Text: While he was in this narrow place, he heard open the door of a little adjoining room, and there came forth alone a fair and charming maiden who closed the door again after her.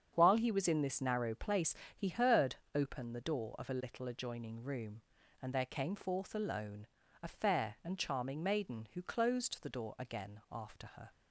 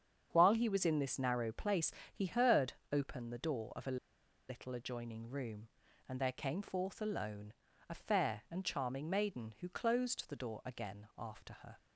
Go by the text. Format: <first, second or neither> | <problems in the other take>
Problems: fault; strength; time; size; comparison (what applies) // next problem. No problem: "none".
first | starts louder than the rest; strong; until 1.3 s; 8 dB; strong in the first // pauses between "heard" and "open"; slight; at 2.7 s; 0.18 s long; slight in the first // pauses between "a" and "little"; noticeable; at 3.9 s; 0.52 s long // pauses between "alone" and "a"; slight; at 7.5 s; 0.34 s long; slight in the first